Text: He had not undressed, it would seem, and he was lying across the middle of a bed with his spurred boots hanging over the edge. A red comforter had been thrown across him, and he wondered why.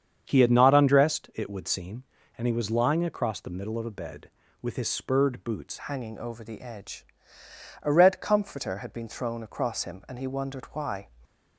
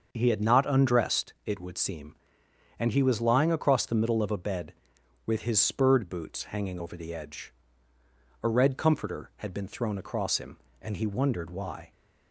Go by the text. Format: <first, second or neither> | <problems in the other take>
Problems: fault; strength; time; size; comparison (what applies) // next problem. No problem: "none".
second | starts louder than the rest; strong; until 1.2 s; 7.5 dB; also in the second // changes voice at "hanging"; from 5.8 s on; 5.2 s long